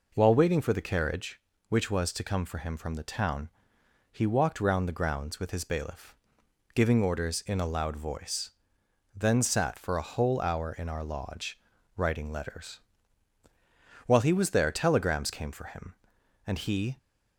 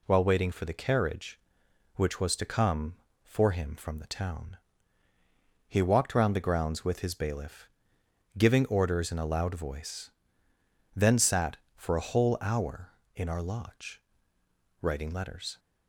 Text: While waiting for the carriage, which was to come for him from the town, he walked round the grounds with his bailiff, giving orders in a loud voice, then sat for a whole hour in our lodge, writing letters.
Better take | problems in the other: second | goes on to say "While he was there telegrams came for him and he"; strong; from 14.0 s on; 2.9 s long

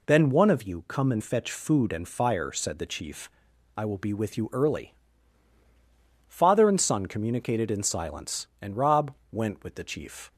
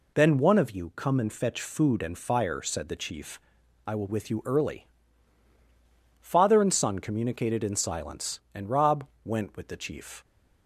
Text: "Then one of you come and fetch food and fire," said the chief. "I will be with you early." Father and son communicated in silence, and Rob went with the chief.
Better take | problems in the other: first | skips "be"; at 4.0 s // pauses between "Rob" and "went"; slight; at 9.0 s; 0.18 s long; slight in the first

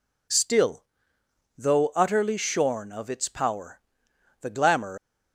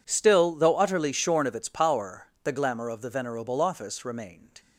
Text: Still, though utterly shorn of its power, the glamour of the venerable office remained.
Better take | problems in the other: second | stops before "of the venerable office remained"; at 4.9 s

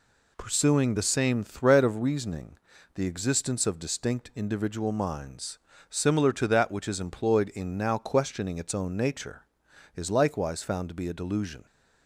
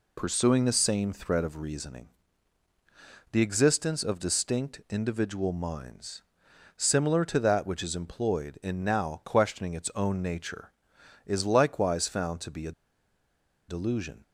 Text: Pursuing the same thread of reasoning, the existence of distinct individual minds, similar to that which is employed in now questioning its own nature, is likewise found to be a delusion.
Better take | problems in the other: first | pauses between "a" and "delusion"; noticeable; at 12.7 s; 0.95 s long

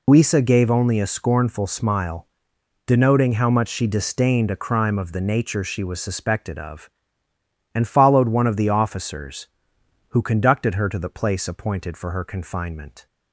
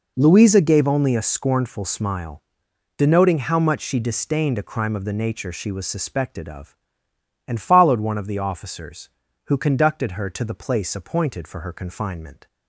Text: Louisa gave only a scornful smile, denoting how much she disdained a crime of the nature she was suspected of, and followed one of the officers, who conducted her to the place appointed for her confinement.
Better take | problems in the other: second | loses the start of "Louisa"; at 0.0 s; 135 ms

